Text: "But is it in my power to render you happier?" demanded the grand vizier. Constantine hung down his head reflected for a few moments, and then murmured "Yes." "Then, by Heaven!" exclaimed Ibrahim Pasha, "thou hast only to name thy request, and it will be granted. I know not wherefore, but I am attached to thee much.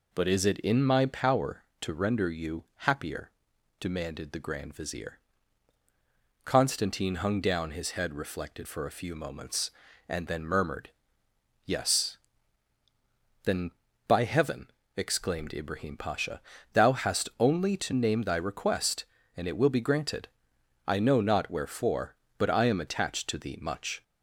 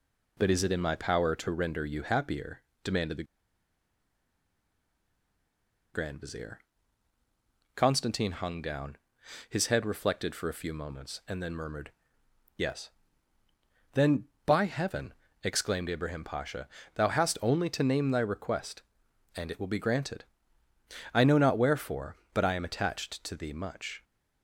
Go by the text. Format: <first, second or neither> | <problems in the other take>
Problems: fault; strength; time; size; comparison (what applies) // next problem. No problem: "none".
first | pauses between "the" and "grand"; strong; at 3.2 s; 2.6 s long // pauses between "down" and "his"; noticeable; at 8.9 s; 0.50 s long // pauses between "murmured" and "Yes"; noticeable; at 11.9 s; 0.66 s long; noticeable in the first